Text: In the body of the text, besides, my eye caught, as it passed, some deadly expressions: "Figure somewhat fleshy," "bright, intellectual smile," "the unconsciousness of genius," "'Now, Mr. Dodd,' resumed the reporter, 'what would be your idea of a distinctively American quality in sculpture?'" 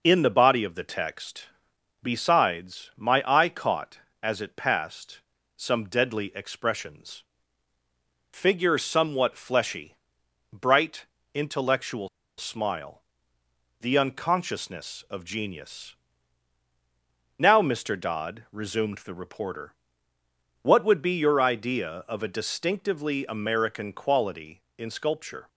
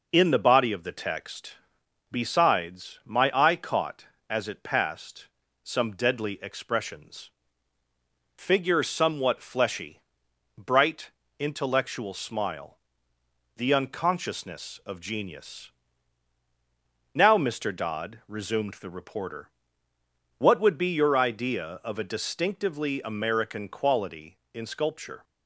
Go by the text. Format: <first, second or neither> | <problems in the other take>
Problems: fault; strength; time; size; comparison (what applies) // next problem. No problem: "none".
second | pauses between "intellectual" and "smile"; slight; at 12.0 s; 0.29 s long